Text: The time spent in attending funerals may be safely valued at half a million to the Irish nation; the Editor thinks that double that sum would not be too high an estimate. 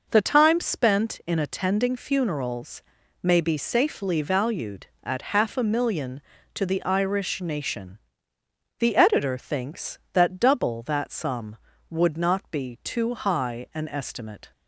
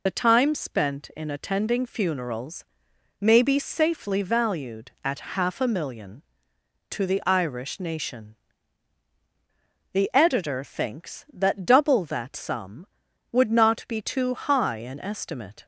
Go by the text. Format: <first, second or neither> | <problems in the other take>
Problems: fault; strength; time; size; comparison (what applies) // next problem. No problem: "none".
first | loses the start of "The"; at 0.0 s; 55 ms // pauses between "funerals" and "may"; noticeable; at 2.6 s; 0.56 s long; also in the first